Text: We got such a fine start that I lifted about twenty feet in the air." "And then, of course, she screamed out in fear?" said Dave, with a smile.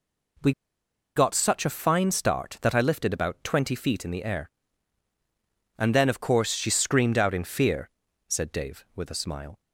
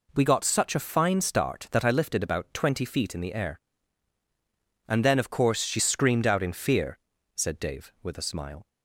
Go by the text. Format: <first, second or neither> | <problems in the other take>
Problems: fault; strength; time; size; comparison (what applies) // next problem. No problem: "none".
second | pauses between "We" and "got"; noticeable; at 0.5 s; 0.64 s long